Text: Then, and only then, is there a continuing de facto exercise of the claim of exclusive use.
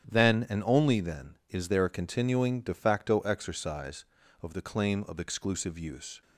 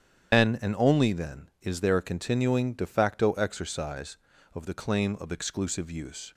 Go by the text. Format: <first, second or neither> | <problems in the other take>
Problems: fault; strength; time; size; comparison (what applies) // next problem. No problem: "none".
first | loses the start of "Then"; at 0.3 s; 155 ms // starts louder than the rest; strong; until 1.4 s; 9.5 dB; strong in the first